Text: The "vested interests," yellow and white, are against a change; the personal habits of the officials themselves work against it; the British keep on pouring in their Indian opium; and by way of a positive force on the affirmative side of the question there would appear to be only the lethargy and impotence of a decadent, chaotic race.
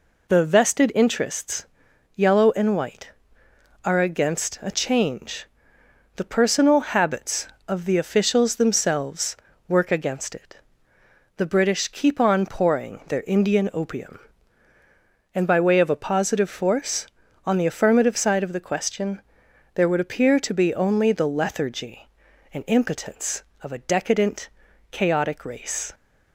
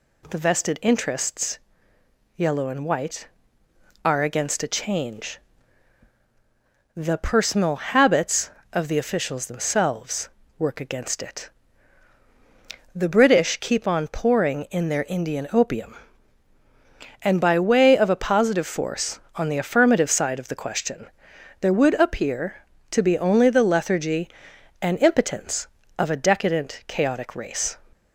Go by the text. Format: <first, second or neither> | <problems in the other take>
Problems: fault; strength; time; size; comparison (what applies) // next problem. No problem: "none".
second | pauses between "themselves" and "work"; slight; at 9.3 s; 0.32 s long; slight in the second // skips "in"; at 13.0 s // pauses between "question" and "there"; noticeable; at 19.2 s; 0.54 s long; noticeable in the second